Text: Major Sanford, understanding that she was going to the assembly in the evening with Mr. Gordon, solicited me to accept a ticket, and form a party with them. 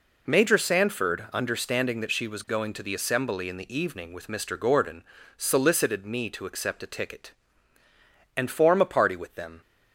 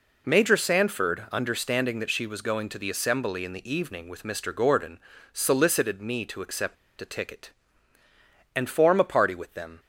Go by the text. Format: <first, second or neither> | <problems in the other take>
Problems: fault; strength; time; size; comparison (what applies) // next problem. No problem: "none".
first | pauses between "accept" and "a"; slight; at 6.7 s; 0.26 s long